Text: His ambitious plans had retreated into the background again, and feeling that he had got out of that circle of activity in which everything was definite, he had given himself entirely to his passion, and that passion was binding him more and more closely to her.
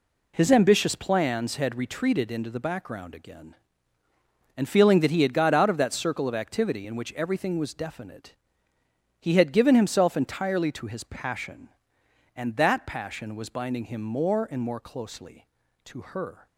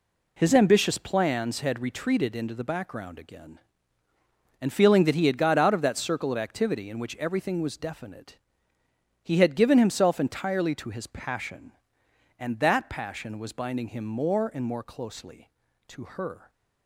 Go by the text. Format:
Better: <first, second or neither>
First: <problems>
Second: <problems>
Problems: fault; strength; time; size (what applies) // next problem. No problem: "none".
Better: neither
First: none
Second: none